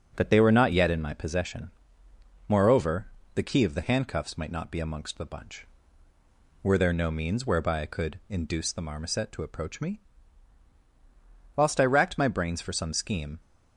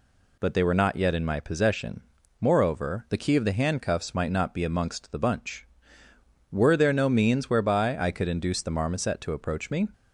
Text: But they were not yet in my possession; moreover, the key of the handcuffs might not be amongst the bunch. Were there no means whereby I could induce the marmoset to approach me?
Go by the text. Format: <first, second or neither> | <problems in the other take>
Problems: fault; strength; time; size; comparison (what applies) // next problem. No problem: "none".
second | starts louder than the rest; strong; until 1.1 s; 7.5 dB // goes on to say "Whilst I racked my brains for some scheme"; strong; from 11.5 s on; 1.8 s long